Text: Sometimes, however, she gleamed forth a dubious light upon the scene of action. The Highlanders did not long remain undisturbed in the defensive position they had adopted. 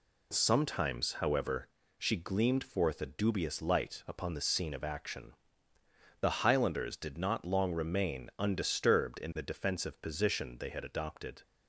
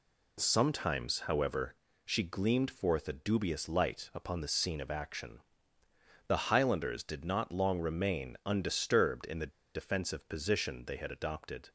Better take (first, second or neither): first